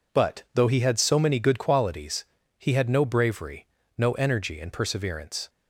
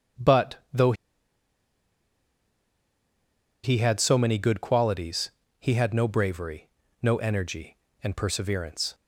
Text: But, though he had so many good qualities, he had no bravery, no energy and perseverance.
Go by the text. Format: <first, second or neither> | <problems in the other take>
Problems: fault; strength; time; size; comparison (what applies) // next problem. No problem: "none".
first | starts louder than the rest; strong; until 4.0 s; 8.5 dB // pauses between "though" and "he"; strong; at 0.9 s; 2.7 s long